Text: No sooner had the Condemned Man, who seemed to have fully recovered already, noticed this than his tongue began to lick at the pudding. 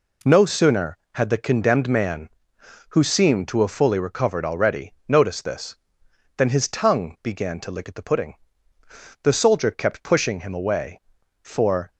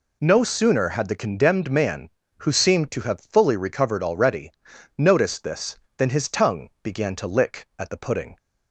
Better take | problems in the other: second | goes on to say "The Soldier kept pushing him away for"; strong; from 9.2 s on; 2.6 s long

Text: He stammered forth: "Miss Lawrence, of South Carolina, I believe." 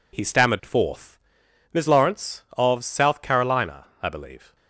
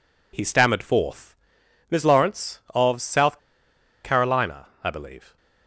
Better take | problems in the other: first | pauses between "South" and "Carolina"; noticeable; at 3.3 s; 0.65 s long

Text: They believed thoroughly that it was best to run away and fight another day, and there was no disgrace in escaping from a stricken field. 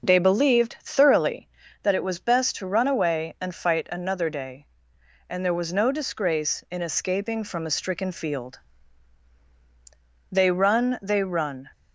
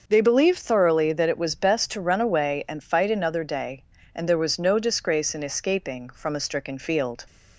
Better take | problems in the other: second | starts louder than the rest; noticeable; until 1.1 s; 6 dB; also in the second // goes on to say "They run They run"; from 10.3 s on; 1.4 s long

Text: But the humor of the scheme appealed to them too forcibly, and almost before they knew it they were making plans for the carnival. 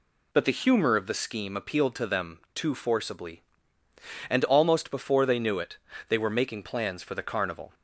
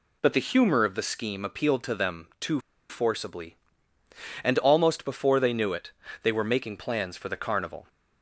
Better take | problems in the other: first | pauses between "too" and "forcibly"; slight; at 2.5 s; 0.30 s long // pauses between "it" and "they"; slight; at 5.9 s; 0.30 s long; slight in the first

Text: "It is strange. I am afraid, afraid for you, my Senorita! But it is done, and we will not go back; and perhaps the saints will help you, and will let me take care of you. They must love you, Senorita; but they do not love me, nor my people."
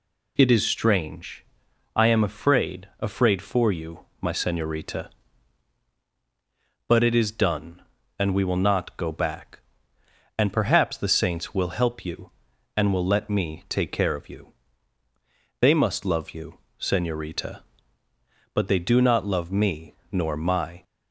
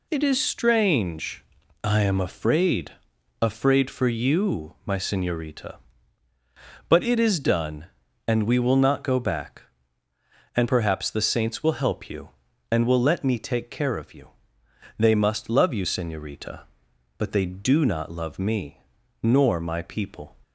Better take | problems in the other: second | stops before "people"; at 20.8 s

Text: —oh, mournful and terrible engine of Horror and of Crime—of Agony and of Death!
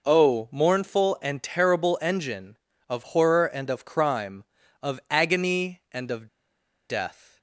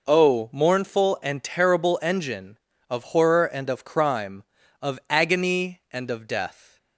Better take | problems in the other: second | pauses between "of" and "Death"; noticeable; at 6.2 s; 0.61 s long

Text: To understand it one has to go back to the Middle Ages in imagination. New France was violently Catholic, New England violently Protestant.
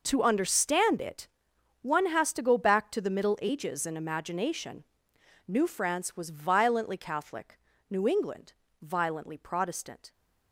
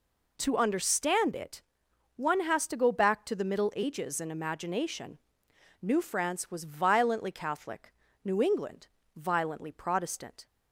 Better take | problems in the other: second | gets quieter; strong; throughout; 14 dB // pauses between "it" and "one"; noticeable; at 1.2 s; 0.54 s long; noticeable in the second // pauses between "England" and "violently"; slight; at 8.5 s; 0.30 s long; slight in the second

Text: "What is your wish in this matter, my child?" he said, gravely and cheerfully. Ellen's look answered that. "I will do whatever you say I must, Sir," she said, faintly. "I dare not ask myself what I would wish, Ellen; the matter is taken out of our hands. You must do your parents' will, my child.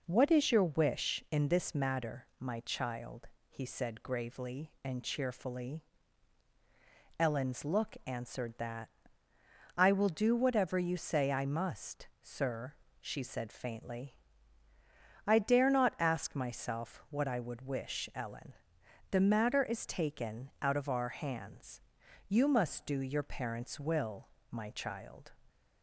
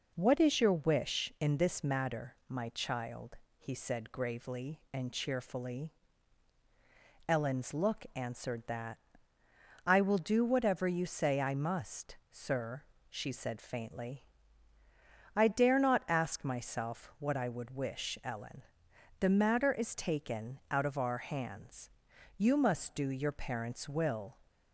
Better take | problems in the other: first | stops before "my child"; at 24.4 s

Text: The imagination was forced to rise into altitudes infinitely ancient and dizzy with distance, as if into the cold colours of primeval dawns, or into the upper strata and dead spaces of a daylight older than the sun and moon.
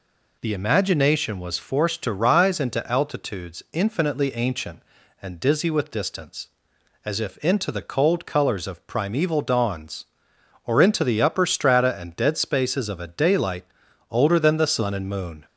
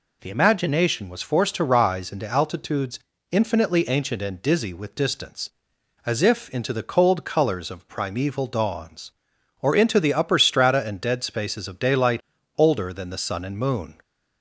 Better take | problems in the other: first | pauses between "altitudes" and "infinitely"; slight; at 2.9 s; 0.32 s long // skips "a"; at 11.7 s // pauses between "daylight" and "older"; slight; at 12.2 s; 0.36 s long; noticeable in the first

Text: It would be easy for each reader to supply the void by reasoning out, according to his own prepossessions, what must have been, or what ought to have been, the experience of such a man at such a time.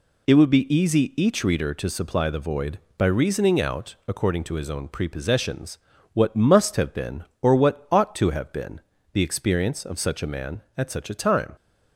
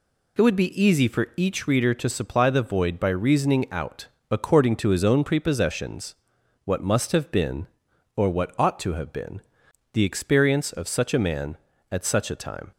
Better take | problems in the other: second | skips "for"; at 1.1 s

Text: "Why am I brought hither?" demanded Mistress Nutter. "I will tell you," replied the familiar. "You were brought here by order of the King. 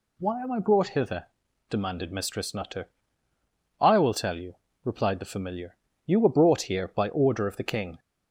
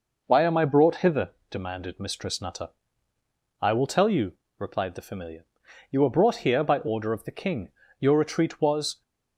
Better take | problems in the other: first | goes on to say "Your retreat was"; noticeable; from 7.9 s on; 1.0 s long

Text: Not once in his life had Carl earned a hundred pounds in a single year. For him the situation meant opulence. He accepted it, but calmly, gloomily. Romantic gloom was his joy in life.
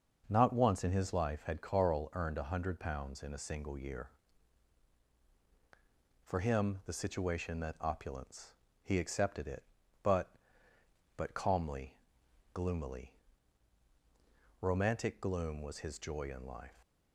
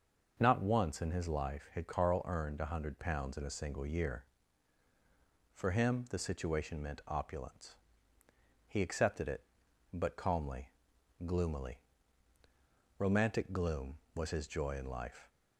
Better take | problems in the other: second | starts louder than the rest; until 1.2 s; 6 dB; noticeable in the second // says "but" twice; at 11.1 s

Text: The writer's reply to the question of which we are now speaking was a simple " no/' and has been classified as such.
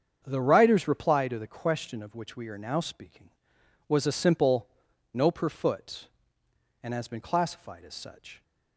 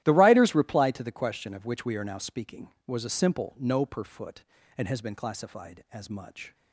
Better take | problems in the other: first | starts louder than the rest; strong; until 1.0 s; 14.5 dB; strong in the first // says "much" for "such"; at 6.1 s

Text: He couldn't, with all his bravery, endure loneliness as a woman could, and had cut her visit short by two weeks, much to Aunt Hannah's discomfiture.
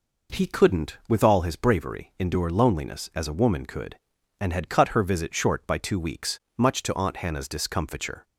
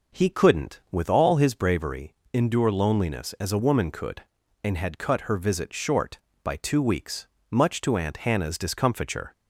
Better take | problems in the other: neither | none

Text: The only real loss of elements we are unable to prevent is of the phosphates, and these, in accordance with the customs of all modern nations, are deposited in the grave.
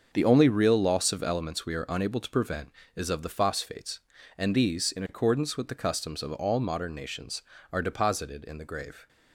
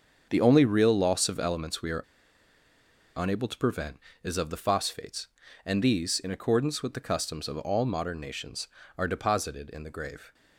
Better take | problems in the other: first | starts louder than the rest; until 1.3 s; 7 dB; also in the first // pauses between "are" and "unable"; at 2.0 s; 1.1 s long

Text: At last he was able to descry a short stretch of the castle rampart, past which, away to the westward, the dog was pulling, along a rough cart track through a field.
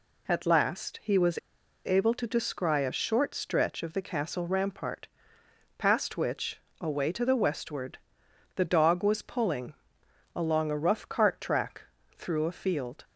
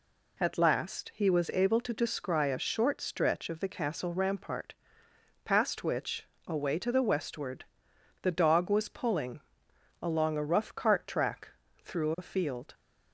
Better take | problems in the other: second | pauses between "was" and "able"; noticeable; at 1.3 s; 0.47 s long // pauses between "track" and "through"; slight; at 11.8 s; 0.36 s long; slight in the second

